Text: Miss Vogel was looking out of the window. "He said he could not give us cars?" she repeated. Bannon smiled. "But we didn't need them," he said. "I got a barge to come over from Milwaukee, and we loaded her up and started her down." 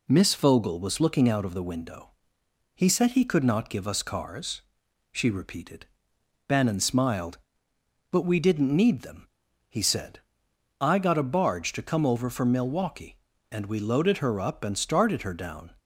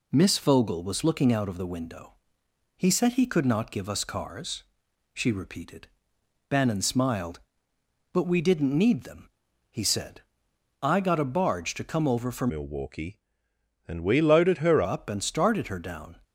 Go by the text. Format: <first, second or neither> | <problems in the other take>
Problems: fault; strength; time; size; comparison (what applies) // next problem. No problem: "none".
first | changes voice from "Milwaukee" to "her"; from 12.4 to 14.8 s; 2.4 s long